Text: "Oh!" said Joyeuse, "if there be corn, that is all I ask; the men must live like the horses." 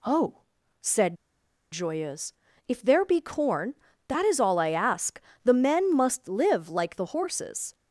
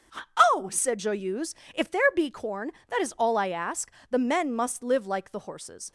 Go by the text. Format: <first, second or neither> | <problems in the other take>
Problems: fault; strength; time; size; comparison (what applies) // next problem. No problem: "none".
second | pauses between "said" and "Joyeuse"; noticeable; at 1.1 s; 0.57 s long